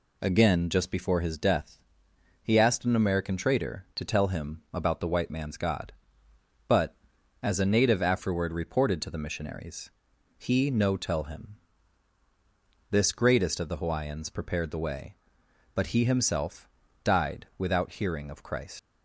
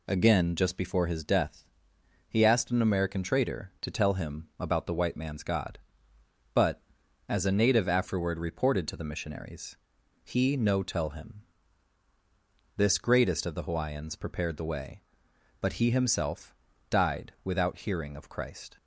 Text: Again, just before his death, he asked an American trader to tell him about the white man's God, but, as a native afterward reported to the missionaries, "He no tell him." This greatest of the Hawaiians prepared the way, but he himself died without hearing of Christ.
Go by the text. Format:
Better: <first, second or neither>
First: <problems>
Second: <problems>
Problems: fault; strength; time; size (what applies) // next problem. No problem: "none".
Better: second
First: pauses between "himself" and "died"; slight; at 16.6 s; 0.36 s long // leaves "Christ" unfinished; at 18.7 s; 110 ms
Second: pauses between "himself" and "died"; slight; at 16.5 s; 0.36 s long